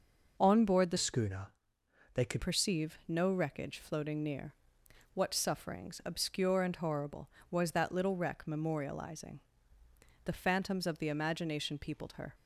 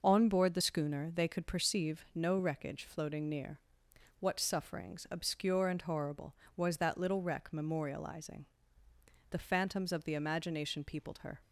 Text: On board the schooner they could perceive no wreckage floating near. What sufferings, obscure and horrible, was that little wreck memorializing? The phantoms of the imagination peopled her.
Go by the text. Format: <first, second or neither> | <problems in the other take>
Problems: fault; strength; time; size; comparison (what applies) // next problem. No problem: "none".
second | changes voice from "schooner" to "could"; from 0.9 to 2.4 s; 1.5 s long // pauses between "schooner" and "they"; noticeable; at 1.5 s; 0.60 s long